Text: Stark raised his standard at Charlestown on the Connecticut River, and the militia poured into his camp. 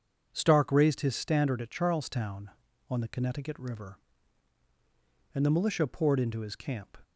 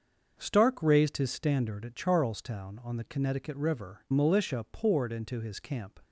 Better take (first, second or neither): first